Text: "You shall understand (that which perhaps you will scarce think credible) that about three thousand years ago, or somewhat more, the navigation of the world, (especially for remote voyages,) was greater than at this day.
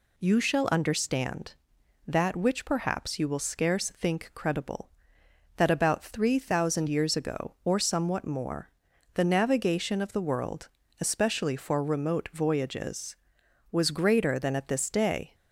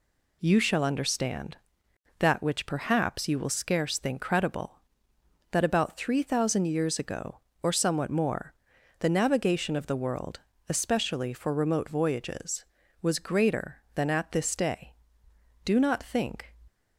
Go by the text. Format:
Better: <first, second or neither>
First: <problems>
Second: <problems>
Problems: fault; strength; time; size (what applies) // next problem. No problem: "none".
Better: first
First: none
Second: goes on to say "Do not think"; noticeable; from 15.6 s on; 0.88 s long